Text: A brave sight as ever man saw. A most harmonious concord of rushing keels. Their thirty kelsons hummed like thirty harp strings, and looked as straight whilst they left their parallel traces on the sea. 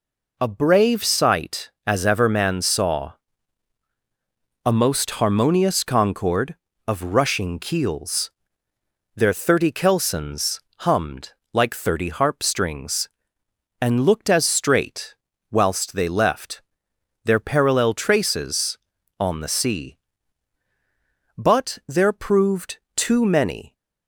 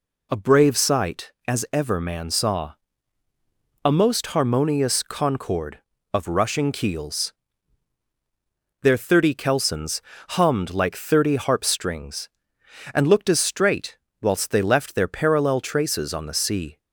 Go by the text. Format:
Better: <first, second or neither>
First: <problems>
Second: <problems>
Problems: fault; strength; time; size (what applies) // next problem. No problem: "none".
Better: second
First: pauses between "kelsons" and "hummed"; slight; at 10.5 s; 0.22 s long // pauses between "hummed" and "like"; slight; at 11.3 s; 0.22 s long // pauses between "straight" and "whilst"; slight; at 15.1 s; 0.34 s long // pauses between "left" and "their"; noticeable; at 16.6 s; 0.64 s long // goes on to say "But there proved too many"; strong; from 21.3 s on; 2.3 s long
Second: pauses between "kelsons" and "hummed"; slight; at 10.0 s; 0.28 s long // pauses between "straight" and "whilst"; slight; at 13.9 s; 0.24 s long